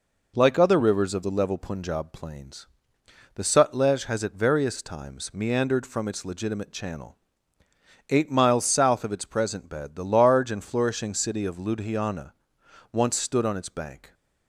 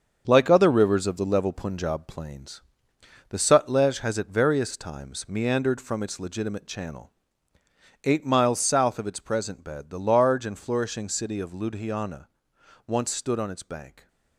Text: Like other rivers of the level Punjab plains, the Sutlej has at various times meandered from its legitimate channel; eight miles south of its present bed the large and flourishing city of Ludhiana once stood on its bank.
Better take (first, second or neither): first